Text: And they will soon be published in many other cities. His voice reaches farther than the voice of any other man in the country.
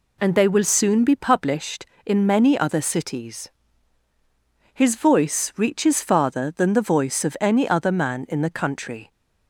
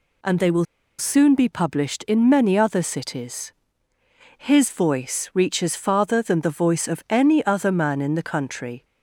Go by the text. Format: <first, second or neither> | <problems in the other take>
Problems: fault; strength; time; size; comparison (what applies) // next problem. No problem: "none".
first | pauses between "will" and "soon"; slight; at 0.6 s; 0.33 s long